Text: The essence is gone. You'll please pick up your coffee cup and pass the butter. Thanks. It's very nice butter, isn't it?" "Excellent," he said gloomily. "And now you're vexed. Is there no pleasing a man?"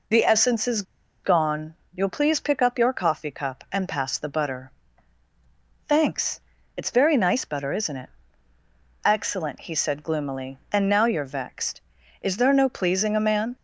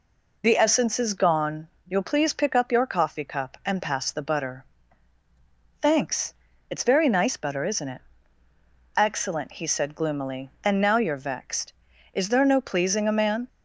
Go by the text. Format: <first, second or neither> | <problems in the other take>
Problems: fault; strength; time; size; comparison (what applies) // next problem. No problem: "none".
second | pauses between "is" and "gone"; at 0.8 s; 0.41 s long